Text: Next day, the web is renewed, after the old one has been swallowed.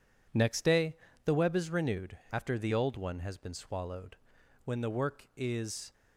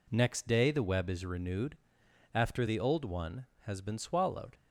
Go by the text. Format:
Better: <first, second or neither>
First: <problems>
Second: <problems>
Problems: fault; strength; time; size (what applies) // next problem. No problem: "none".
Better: second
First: goes on to say "When the work is"; noticeable; from 4.6 s on; 1.2 s long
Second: none